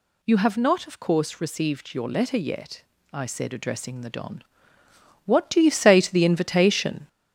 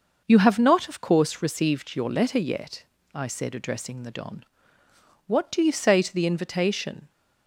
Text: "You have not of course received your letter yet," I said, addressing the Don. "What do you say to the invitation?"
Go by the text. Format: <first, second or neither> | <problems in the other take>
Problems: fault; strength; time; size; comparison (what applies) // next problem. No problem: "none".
second | gets louder; noticeable; throughout; 4.5 dB